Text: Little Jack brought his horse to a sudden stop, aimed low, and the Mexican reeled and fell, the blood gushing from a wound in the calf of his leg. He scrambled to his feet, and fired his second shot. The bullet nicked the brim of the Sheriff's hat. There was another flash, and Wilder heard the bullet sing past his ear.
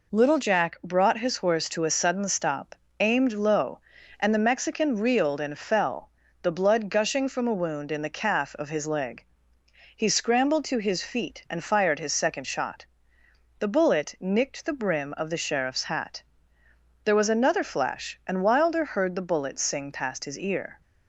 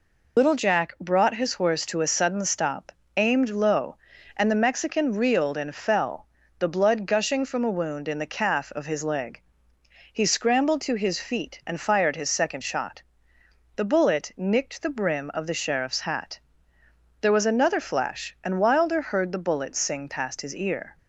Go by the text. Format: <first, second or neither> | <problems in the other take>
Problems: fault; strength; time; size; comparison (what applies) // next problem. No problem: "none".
first | loses the start of "Little"; at 0.3 s; 90 ms